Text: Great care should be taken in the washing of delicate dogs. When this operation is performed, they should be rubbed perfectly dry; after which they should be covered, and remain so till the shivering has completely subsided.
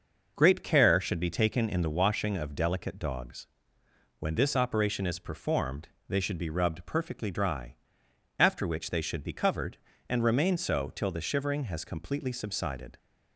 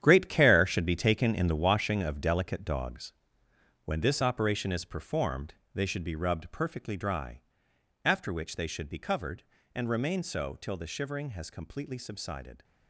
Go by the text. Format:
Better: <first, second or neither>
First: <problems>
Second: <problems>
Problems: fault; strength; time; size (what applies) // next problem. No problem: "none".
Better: first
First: starts louder than the rest; noticeable; until 1.3 s; 6 dB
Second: gets quieter; strong; throughout; 12 dB // starts louder than the rest; strong; until 1.0 s; 10 dB